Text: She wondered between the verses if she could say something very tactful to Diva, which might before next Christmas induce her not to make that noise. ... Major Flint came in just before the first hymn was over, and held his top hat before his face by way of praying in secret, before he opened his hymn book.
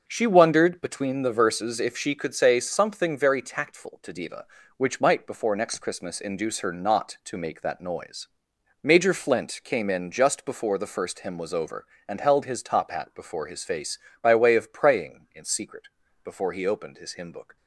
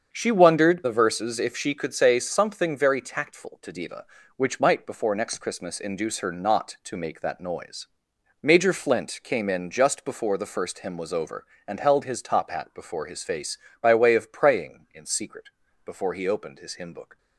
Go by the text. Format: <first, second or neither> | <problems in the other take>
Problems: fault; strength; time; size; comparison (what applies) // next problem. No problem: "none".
first | starts louder than the rest; until 1.1 s; 7 dB; noticeable in the first // skips "between"; at 0.8 s